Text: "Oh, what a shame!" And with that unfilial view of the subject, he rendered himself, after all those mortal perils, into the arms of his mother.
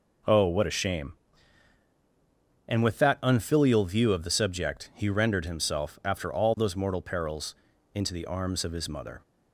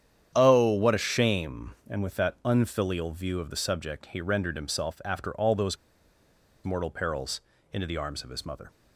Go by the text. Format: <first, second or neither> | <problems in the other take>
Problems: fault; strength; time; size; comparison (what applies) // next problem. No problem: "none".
first | starts louder than the rest; strong; until 1.3 s; 9 dB // pauses between "those" and "mortal"; noticeable; at 5.7 s; 0.87 s long